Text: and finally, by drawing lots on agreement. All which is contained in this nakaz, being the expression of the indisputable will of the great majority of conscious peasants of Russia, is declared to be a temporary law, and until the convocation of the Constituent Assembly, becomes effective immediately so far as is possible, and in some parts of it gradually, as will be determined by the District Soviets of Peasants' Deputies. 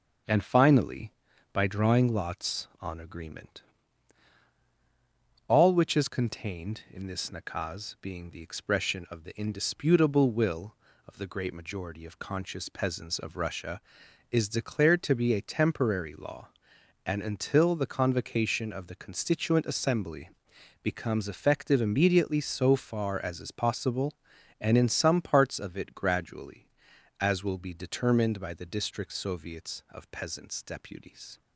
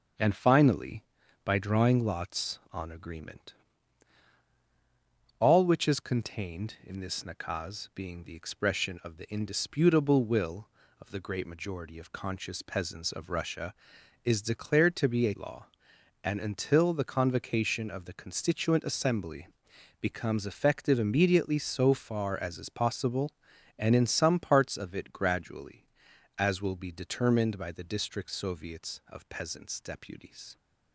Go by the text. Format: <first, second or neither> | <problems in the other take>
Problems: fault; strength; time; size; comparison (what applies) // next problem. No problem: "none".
first | starts louder than the rest; until 1.5 s; 6 dB; also in the first // skips "temporary"; at 15.3 s